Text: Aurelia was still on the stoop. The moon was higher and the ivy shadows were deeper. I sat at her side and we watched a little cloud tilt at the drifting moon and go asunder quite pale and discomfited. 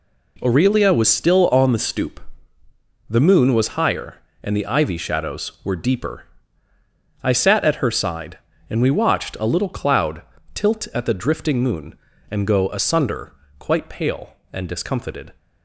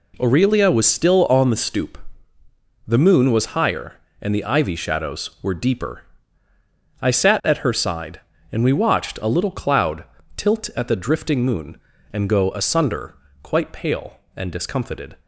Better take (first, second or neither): neither